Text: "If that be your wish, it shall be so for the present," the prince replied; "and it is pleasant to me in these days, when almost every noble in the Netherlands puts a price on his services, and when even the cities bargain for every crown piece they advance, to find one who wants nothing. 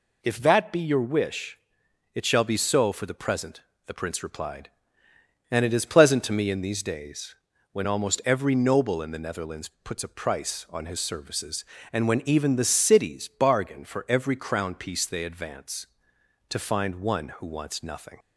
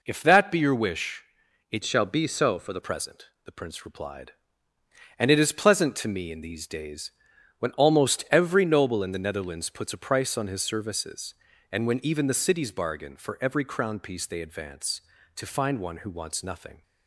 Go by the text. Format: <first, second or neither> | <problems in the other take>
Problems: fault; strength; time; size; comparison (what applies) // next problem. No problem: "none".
first | changes voice from "shall" to "the"; from 1.8 to 2.8 s; 1.0 s long